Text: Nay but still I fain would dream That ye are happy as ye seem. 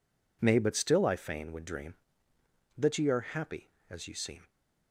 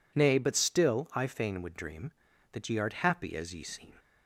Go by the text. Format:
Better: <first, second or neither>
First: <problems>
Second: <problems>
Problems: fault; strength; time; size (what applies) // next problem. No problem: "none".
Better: first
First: none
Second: says "art" for "are"; at 2.7 s